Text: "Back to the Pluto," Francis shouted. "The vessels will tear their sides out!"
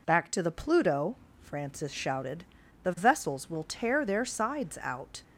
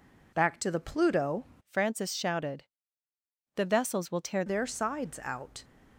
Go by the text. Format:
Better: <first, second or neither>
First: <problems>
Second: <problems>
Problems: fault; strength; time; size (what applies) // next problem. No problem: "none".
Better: first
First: none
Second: changes voice from "Francis" to "tear"; from 1.6 to 4.4 s; 2.8 s long